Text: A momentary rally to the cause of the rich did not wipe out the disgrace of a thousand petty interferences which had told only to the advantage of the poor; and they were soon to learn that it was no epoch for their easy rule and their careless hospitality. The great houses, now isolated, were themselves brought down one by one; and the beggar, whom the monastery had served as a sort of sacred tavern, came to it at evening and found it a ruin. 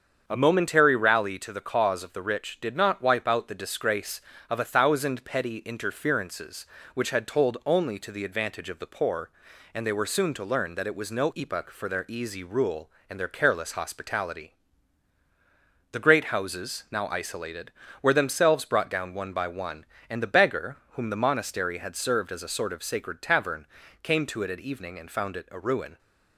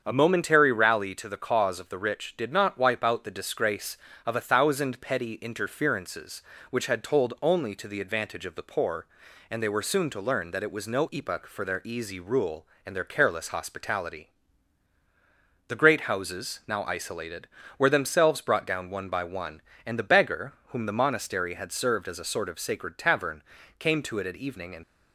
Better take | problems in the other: first | starts louder than the rest; strong; until 1.0 s; 7.5 dB; strong in the first // stops before "found it a ruin"; at 24.8 s

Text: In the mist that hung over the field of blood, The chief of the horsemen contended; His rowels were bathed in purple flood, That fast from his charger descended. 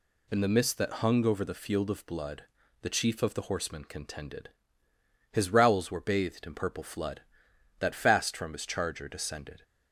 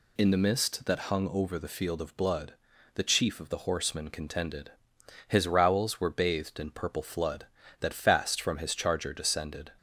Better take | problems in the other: neither | none

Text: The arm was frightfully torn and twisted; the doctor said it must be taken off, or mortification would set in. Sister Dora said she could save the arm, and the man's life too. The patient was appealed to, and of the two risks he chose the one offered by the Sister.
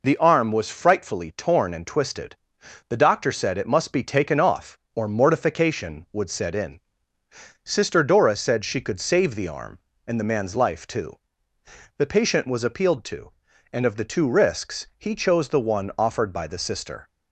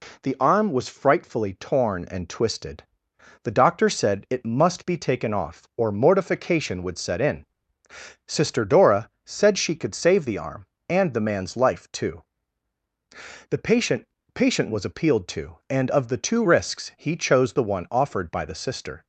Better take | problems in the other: first | says "patient" twice; at 14.3 s

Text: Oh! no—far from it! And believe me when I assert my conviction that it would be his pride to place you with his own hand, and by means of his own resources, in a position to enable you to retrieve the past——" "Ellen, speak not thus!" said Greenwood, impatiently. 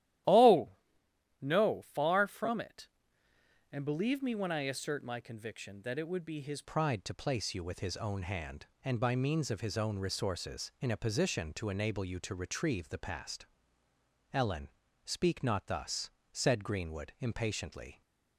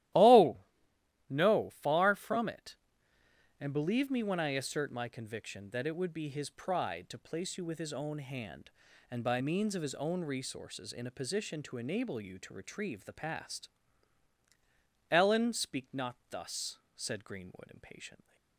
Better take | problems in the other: second | starts louder than the rest; strong; until 1.9 s; 13 dB; strong in the second // changes voice at "pride"; from 6.6 s on; 11.4 s long

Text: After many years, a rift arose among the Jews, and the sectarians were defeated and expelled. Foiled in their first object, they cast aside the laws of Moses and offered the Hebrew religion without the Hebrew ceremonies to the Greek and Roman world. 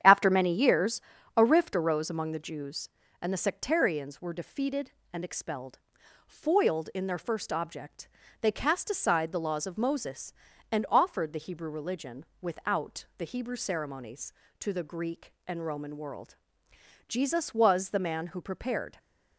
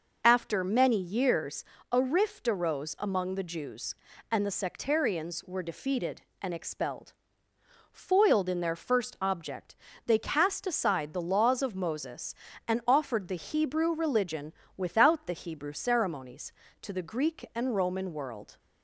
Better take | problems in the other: second | starts louder than the rest; strong; until 1.4 s; 9 dB // pauses between "religion" and "without"; slight; at 12.2 s; 0.16 s long; slight in the second // goes on to say "Jesus was the man who prepared"; strong; from 17.0 s on; 1.9 s long

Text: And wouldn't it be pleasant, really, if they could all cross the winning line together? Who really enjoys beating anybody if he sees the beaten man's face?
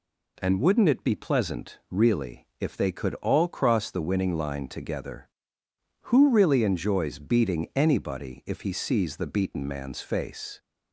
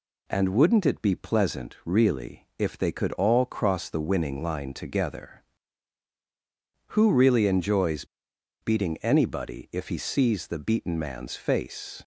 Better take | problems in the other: first | pauses between "enjoys" and "beating"; noticeable; at 8.0 s; 0.57 s long

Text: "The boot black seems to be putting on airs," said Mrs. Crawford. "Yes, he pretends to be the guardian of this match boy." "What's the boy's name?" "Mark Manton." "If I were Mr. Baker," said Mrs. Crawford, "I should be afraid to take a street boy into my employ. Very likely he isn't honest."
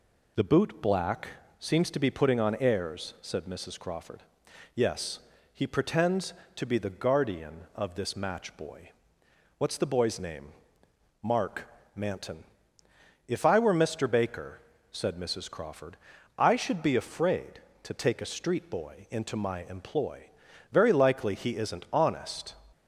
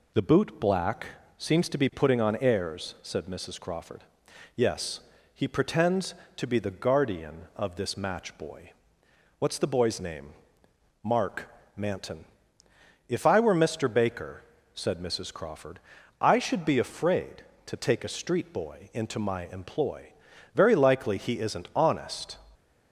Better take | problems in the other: neither | pauses between "black" and "seems"; slight; the same in both // pauses between "Mark" and "Manton"; slight; the same in both

